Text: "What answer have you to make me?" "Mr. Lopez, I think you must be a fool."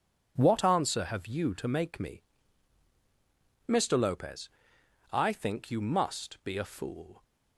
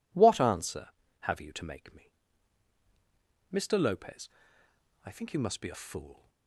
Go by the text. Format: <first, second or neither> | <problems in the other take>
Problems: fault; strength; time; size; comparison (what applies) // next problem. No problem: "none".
neither | none